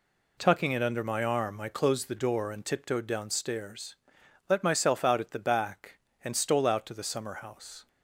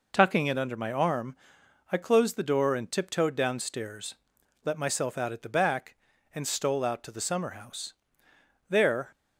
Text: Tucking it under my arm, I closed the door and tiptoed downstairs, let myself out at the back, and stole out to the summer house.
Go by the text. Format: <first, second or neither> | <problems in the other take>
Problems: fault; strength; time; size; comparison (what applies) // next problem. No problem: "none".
first | goes on to say "There"; slight; from 8.6 s on; 0.42 s long